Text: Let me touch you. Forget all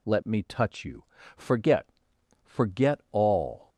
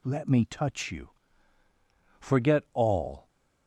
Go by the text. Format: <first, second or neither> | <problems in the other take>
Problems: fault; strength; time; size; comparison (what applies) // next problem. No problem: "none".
second | says "Forget" twice; at 2.4 s